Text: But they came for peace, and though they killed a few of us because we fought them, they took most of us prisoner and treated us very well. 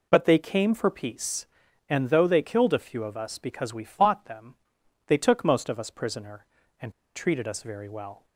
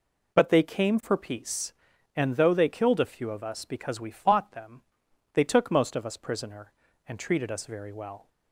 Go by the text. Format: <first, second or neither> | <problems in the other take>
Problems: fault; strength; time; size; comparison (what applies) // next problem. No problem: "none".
second | pauses between "and" and "treated"; slight; at 6.9 s; 0.23 s long